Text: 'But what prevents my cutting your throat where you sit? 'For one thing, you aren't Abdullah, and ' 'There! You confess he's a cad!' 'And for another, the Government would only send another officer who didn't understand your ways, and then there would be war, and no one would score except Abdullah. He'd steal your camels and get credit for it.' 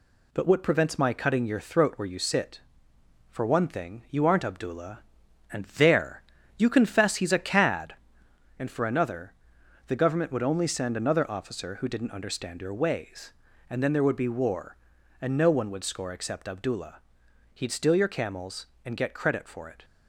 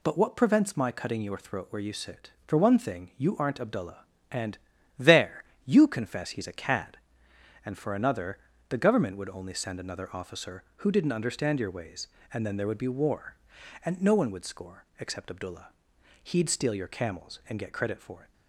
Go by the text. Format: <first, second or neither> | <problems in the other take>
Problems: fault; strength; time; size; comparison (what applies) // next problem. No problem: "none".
neither | none